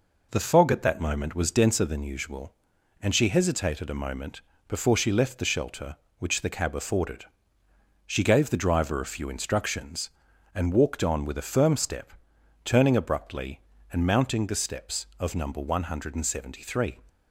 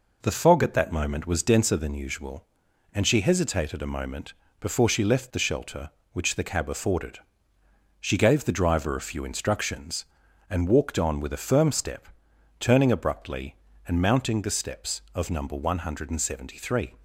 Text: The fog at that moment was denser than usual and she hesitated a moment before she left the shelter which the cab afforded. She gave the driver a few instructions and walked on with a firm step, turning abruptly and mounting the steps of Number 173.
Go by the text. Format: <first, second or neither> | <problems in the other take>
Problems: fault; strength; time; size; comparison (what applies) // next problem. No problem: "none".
neither | pauses between "moment" and "before"; slight; the same in both